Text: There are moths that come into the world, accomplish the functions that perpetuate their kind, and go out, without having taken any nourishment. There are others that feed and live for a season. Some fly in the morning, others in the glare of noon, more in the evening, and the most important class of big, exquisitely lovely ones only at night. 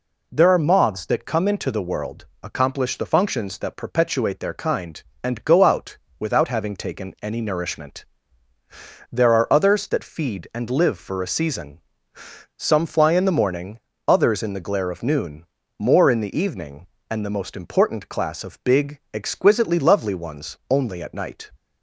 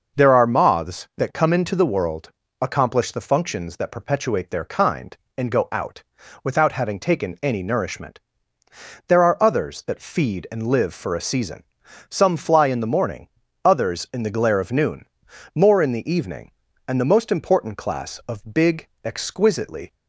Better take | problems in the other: first | stops before "lovely ones only at night"; at 19.9 s

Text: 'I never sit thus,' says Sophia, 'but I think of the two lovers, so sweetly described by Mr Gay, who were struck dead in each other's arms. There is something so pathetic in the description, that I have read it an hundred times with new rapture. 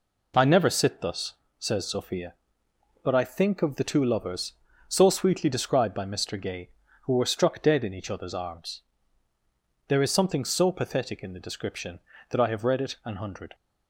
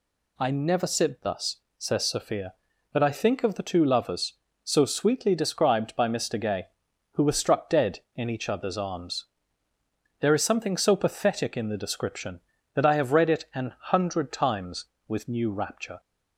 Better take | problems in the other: second | stops before "times with new rapture"; at 13.5 s

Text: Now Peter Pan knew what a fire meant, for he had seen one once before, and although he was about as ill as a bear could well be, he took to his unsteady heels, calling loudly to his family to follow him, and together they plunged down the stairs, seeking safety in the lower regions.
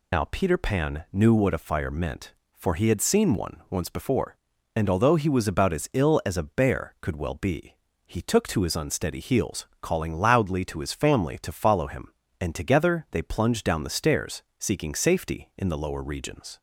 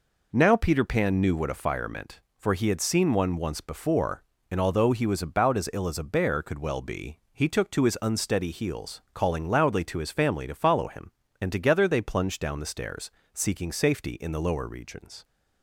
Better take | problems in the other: second | loses the start of "Now"; at 0.1 s; 100 ms

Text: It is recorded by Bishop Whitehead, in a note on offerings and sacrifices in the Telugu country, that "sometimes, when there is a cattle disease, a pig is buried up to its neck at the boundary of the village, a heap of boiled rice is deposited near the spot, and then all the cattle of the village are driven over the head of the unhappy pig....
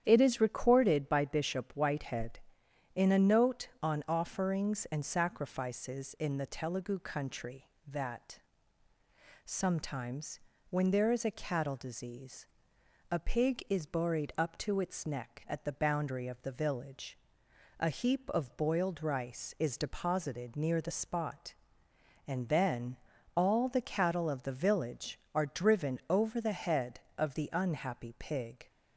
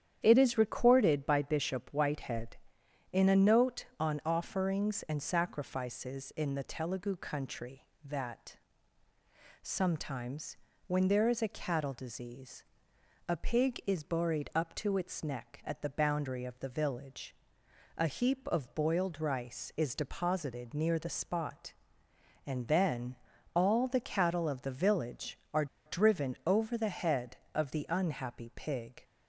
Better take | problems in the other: first | starts louder than the rest; strong; until 1.2 s; 9.5 dB; strong in the first // pauses between "that" and "sometimes"; at 8.5 s; 1.0 s long; also in the first // pauses between "then" and "all"; at 23.1 s; 0.40 s long; also in the first // pauses between "are" and "driven"; slight; at 25.6 s; 0.20 s long

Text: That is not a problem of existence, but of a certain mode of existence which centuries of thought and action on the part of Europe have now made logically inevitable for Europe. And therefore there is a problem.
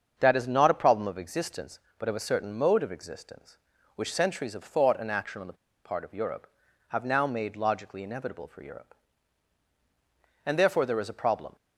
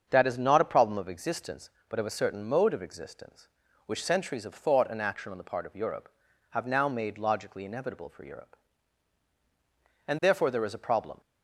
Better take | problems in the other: second | starts louder than the rest; until 1.1 s; 7 dB; also in the second // pauses between "the" and "part"; slight; at 5.5 s; 0.31 s long

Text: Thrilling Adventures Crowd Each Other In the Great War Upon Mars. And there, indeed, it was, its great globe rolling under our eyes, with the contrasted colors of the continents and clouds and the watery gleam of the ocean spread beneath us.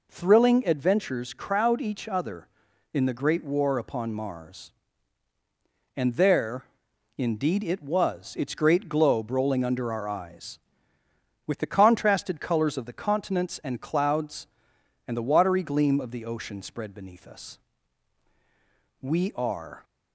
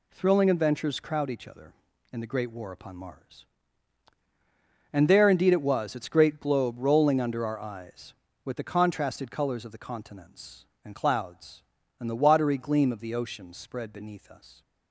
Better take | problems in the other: second | goes on to say "We are"; noticeable; from 19.0 s on; 0.82 s long

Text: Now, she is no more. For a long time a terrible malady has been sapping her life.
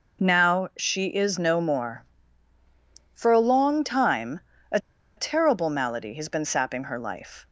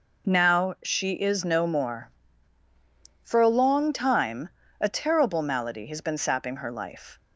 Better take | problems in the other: second | pauses between "time" and "a"; slight; at 4.4 s; 0.28 s long; slight in the second // pauses between "a" and "terrible"; at 4.7 s; 0.39 s long

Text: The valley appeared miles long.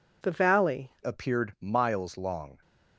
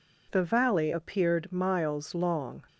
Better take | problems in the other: second | changes voice at "appeared"; from 1.0 s on; 1.5 s long

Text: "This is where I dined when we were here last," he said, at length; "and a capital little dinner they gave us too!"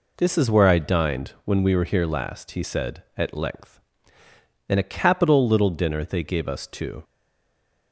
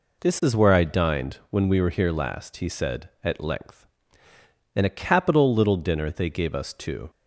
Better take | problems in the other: second | stays silent after the last word; slight; from 7.0 s on; 0.9 s long

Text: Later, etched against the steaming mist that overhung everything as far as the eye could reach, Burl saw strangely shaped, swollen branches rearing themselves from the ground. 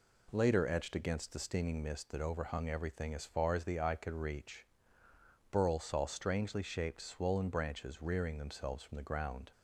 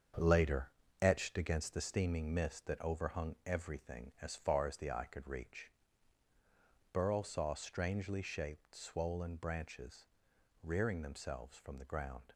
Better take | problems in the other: first | gets quieter; strong; throughout; 8.5 dB // pauses between "branches" and "rearing"; noticeable; at 10.0 s; 0.56 s long

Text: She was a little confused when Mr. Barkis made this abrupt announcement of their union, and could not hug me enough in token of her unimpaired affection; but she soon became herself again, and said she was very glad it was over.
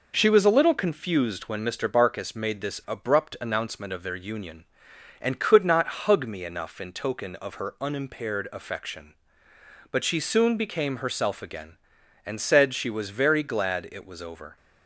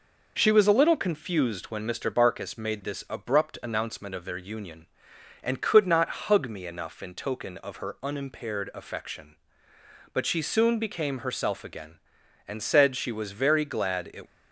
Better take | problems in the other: first | stops before "was over"; at 14.2 s

